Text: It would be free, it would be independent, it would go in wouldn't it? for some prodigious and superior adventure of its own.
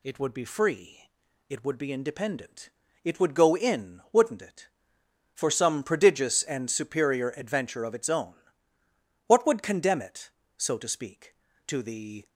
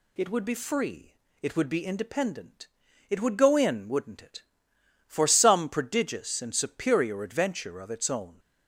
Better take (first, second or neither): second